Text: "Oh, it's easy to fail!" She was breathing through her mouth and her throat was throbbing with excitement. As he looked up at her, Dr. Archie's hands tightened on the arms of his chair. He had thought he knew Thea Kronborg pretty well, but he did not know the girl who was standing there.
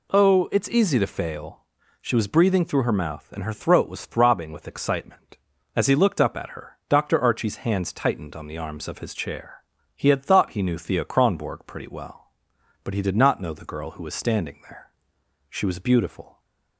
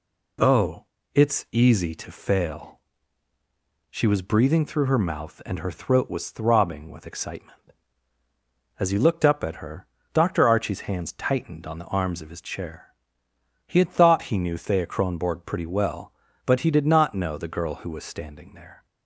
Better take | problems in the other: second | goes on to say "She was beautiful"; noticeable; from 15.4 s on; 0.90 s long

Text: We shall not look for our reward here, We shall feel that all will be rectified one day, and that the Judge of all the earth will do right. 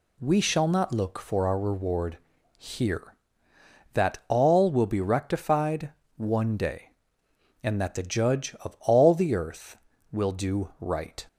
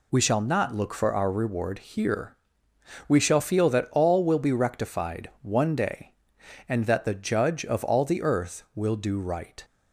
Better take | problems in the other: second | pauses between "reward" and "here"; at 2.1 s; 0.40 s long // skips "We shall feel"; at 3.5 s // pauses between "rectified" and "one"; slight; at 5.9 s; 0.24 s long

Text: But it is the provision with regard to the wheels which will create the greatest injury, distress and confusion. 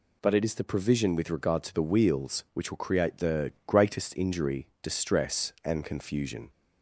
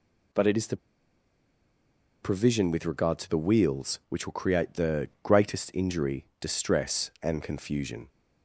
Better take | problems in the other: first | pauses between "the" and "provision"; strong; at 0.7 s; 1.4 s long

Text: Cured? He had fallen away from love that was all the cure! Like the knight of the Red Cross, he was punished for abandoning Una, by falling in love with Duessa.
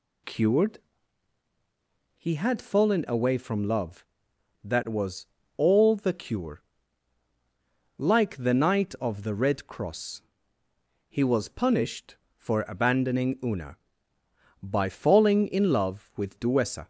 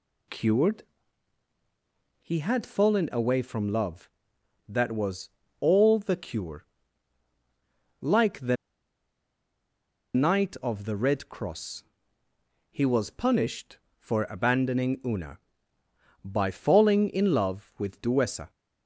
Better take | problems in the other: first | pauses between "was" and "all"; slight; at 5.2 s; 0.30 s long; slight in the first // pauses between "the" and "knight"; strong; at 8.5 s; 1.5 s long

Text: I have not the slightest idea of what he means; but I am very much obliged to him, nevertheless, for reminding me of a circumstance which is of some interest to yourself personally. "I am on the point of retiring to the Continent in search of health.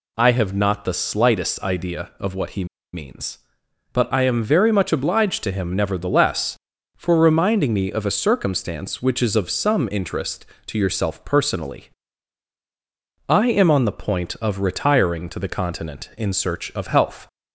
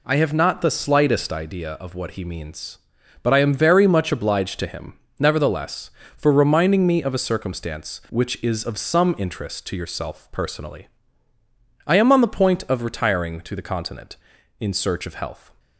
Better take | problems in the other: second | pauses between "he" and "means"; slight; at 2.6 s; 0.28 s long

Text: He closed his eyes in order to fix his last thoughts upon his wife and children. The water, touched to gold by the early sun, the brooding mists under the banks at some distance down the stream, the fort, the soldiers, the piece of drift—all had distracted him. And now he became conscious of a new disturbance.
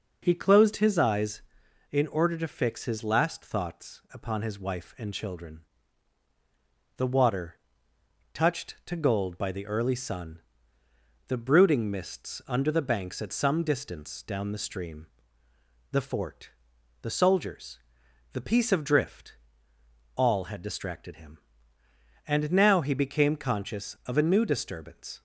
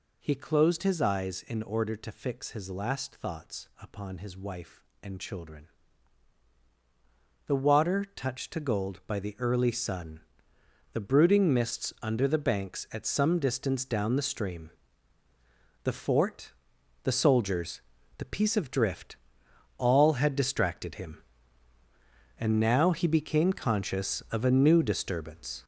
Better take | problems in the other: first | gets louder; throughout; 7 dB

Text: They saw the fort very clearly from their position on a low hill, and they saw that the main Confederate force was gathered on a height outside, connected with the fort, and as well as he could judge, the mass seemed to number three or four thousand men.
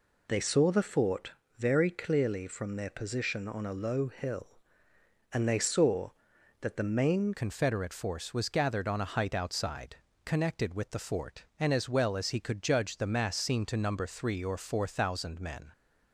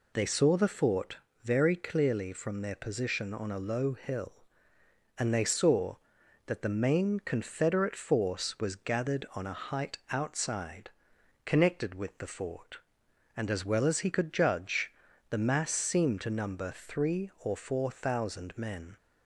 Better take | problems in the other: second | pauses between "fort" and "very"; slight; at 1.3 s; 0.26 s long; slight in the second // changes voice at "Confederate"; from 7.3 s on; 8.4 s long

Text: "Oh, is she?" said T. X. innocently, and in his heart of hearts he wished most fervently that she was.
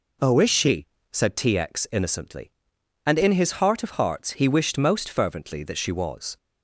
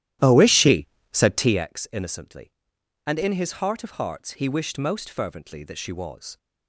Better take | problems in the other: first | starts louder than the rest; strong; until 1.7 s; 13 dB

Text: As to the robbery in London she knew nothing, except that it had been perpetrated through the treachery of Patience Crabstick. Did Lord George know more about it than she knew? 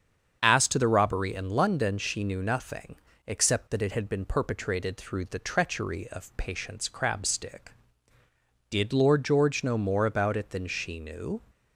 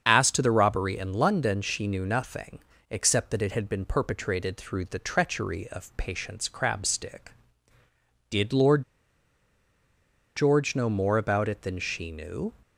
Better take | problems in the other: first | starts louder than the rest; strong; until 1.0 s; 7 dB; strong in the first // pauses between "Lord" and "George"; strong; at 8.8 s; 1.5 s long

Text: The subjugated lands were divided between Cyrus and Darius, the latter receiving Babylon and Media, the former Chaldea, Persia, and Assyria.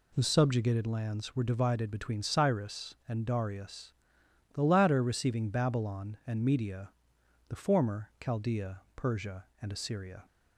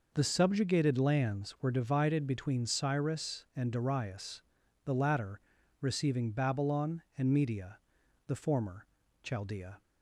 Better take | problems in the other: first | pauses between "latter" and "receiving"; at 5.4 s; 0.40 s long // pauses between "former" and "Chaldea"; slight; at 8.8 s; 0.36 s long // stops before "Persia and Assyria"; at 9.8 s

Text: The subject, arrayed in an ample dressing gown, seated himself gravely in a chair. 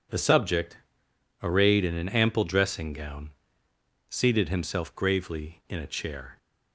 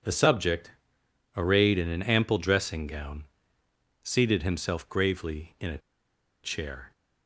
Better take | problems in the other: first | pauses between "a" and "chair"; noticeable; at 5.7 s; 0.65 s long

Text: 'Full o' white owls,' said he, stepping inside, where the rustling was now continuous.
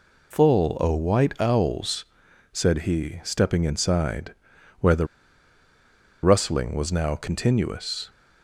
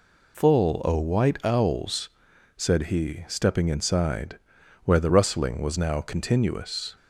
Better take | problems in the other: second | pauses between "the" and "rustling"; at 5.0 s; 1.1 s long

